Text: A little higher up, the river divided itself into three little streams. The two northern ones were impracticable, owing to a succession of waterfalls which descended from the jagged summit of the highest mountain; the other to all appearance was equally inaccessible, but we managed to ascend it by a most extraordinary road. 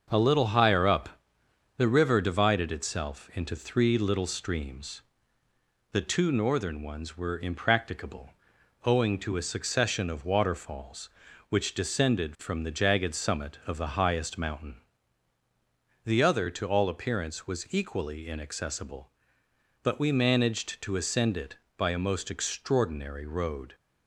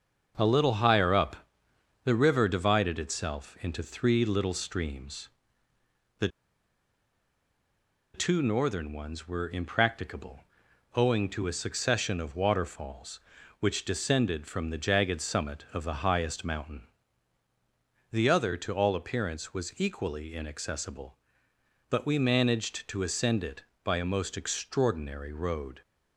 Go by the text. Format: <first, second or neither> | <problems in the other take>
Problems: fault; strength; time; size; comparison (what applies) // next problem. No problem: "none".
first | starts louder than the rest; until 1.3 s; 6.5 dB; also in the first // pauses between "The" and "two"; strong; at 6.2 s; 1.8 s long